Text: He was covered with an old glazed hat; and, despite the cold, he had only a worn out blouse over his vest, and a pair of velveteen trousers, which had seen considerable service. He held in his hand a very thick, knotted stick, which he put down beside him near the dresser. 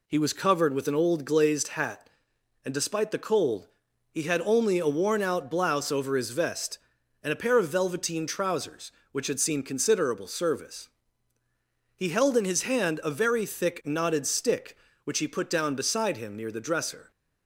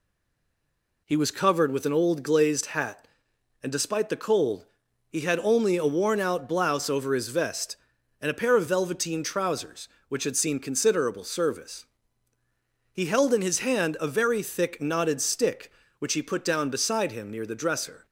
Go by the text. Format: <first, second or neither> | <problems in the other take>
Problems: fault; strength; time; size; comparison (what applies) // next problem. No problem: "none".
first | stays silent before the first word; until 1.0 s; 1.0 s long